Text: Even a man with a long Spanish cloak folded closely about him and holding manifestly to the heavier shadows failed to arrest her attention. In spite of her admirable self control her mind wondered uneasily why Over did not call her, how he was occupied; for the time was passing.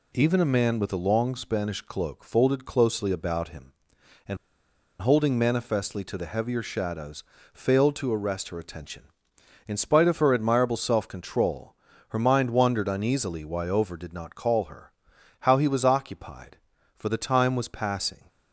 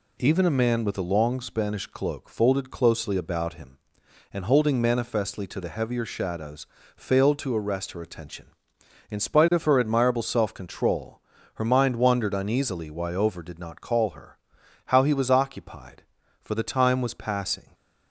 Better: second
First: pauses between "and" and "holding"; noticeable; at 4.3 s; 0.64 s long // pauses between "shadows" and "failed"; slight; at 7.2 s; 0.30 s long // pauses between "control" and "her"; slight; at 11.7 s; 0.36 s long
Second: pauses between "shadows" and "failed"; slight; at 6.6 s; 0.30 s long // pauses between "control" and "her"; slight; at 11.1 s; 0.36 s long

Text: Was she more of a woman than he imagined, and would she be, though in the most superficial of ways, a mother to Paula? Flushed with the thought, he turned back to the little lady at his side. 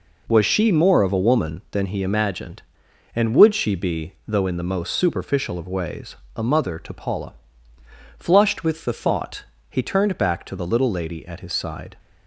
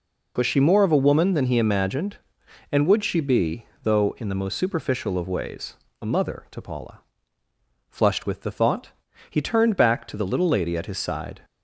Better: neither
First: none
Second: none

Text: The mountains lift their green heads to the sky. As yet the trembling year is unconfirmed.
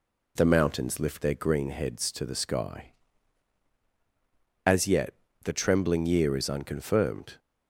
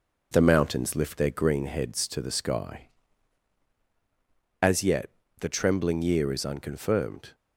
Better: first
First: pauses between "yet" and "the"; slight; at 5.1 s; 0.30 s long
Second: gets quieter; throughout; 4 dB // pauses between "yet" and "the"; slight; at 5.1 s; 0.30 s long

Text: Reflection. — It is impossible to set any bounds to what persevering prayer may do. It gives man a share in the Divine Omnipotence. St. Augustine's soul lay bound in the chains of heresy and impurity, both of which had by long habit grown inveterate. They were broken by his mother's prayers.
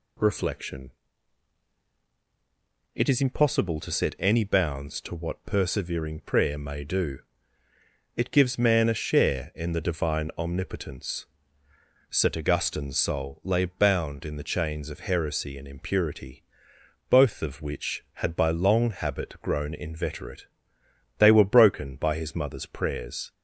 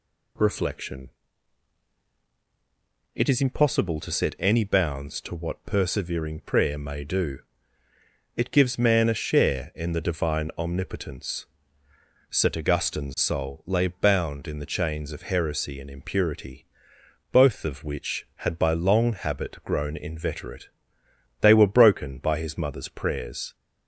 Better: neither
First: none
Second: none

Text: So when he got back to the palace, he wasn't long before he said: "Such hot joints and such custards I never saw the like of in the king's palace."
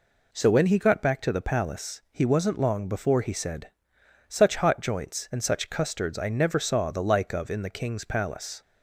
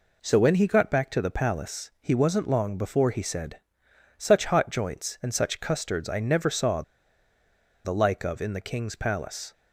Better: first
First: none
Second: pauses between "saw" and "the"; at 6.8 s; 1.0 s long

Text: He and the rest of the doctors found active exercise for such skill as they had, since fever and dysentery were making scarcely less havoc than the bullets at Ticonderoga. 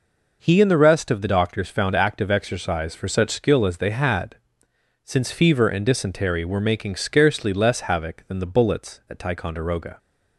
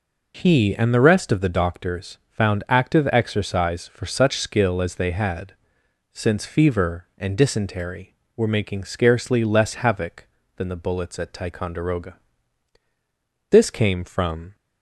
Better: first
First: none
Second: goes on to say "This came from"; noticeable; from 13.5 s on; 1.0 s long

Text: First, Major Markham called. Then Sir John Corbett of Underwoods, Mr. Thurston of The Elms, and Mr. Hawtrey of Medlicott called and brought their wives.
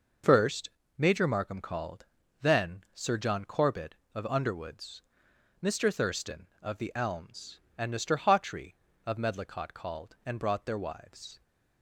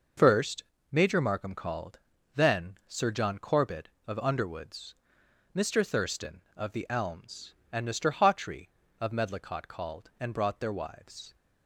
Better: neither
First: none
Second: none

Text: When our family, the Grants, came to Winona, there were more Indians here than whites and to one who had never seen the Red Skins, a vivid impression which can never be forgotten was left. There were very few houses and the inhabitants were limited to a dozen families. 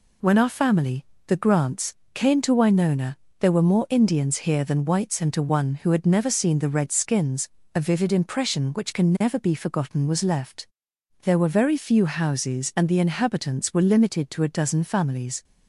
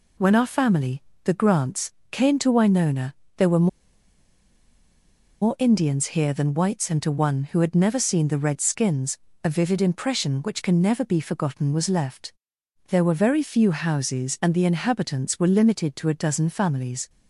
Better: first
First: none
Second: pauses between "were" and "more"; strong; at 3.6 s; 1.7 s long

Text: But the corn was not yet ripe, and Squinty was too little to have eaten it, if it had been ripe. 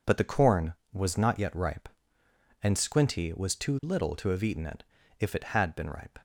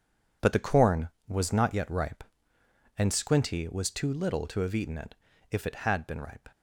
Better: first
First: none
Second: gets quieter; strong; throughout; 10.5 dB

